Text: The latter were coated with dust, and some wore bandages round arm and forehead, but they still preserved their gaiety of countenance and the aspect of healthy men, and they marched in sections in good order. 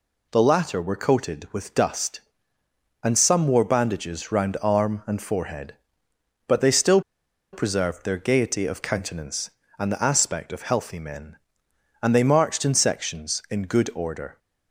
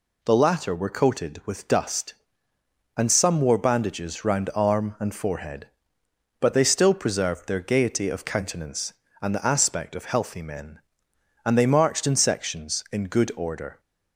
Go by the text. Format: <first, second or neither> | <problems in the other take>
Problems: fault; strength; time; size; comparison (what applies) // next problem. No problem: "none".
second | pauses between "still" and "preserved"; noticeable; at 7.0 s; 0.52 s long